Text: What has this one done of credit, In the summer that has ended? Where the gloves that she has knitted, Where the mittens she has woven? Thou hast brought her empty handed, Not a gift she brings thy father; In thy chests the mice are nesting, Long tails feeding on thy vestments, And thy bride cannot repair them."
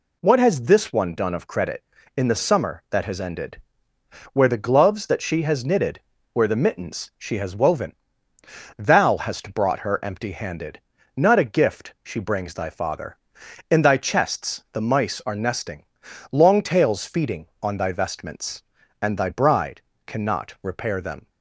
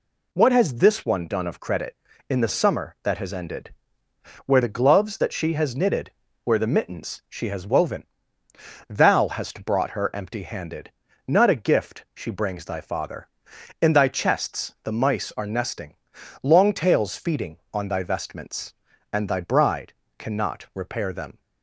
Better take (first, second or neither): neither